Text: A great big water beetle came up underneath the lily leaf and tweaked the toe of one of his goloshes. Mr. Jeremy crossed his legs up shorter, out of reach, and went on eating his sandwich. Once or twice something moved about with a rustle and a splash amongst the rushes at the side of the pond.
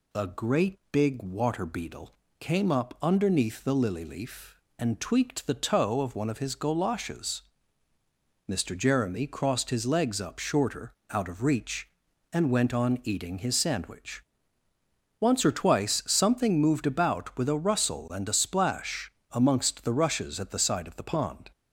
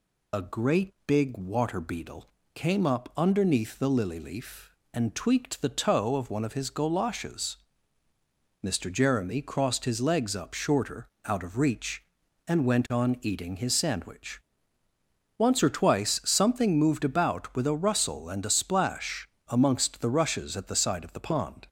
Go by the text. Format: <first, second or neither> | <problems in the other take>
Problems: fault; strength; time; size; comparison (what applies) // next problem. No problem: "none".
first | loses the start of "A"; at 0.3 s; 50 ms // pauses between "beetle" and "came"; slight; at 2.2 s; 0.30 s long; slight in the first // pauses between "splash" and "amongst"; slight; at 19.2 s; 0.20 s long; slight in the first